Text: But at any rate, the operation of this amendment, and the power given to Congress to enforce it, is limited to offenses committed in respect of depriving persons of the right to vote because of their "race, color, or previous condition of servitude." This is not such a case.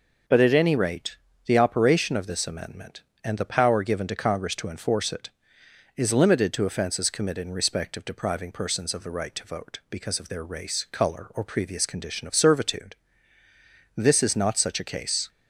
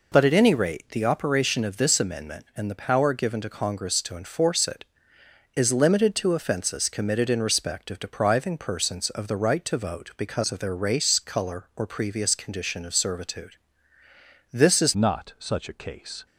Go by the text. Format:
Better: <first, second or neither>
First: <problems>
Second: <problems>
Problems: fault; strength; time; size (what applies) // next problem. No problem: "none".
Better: first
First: none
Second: changes voice at "not"; from 14.9 s on; 1.3 s long